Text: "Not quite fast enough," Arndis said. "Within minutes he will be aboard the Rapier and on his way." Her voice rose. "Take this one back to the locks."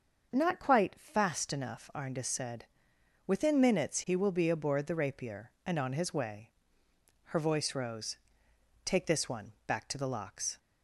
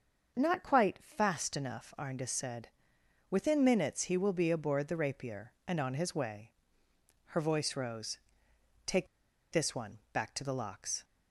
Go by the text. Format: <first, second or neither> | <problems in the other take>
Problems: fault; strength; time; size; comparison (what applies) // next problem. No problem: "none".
first | starts louder than the rest; until 1.4 s; 6.5 dB; also in the first // pauses between "Take" and "this"; noticeable; at 9.0 s; 0.46 s long